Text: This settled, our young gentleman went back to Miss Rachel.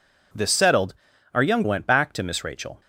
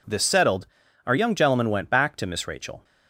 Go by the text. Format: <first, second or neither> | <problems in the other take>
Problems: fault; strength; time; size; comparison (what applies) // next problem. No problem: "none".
second | skips "gentleman"; at 1.6 s